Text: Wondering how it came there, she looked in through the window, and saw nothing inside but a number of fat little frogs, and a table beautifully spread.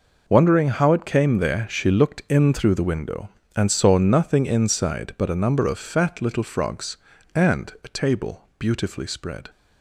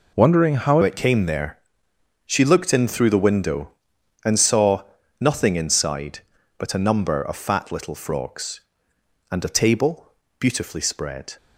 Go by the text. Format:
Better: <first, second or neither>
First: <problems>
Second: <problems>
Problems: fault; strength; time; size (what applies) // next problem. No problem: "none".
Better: first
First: none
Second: changes voice at "it"; from 0.8 s on; 10.5 s long // pauses between "saw" and "nothing"; at 4.8 s; 0.38 s long // pauses between "table" and "beautifully"; slight; at 10.1 s; 0.30 s long